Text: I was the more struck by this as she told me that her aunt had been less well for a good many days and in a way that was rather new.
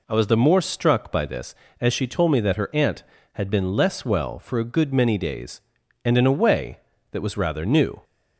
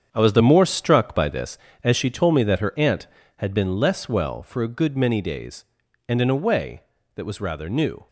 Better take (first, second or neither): first